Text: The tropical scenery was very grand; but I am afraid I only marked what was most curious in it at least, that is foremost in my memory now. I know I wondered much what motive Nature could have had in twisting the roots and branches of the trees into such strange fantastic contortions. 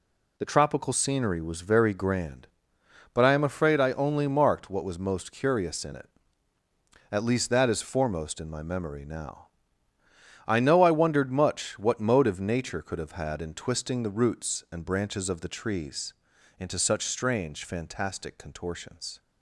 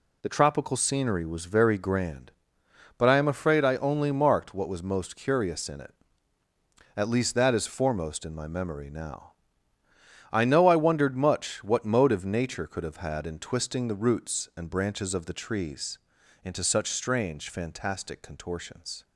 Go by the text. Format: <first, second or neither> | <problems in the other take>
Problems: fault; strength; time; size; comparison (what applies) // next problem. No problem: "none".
neither | pauses between "trees" and "into"; the same in both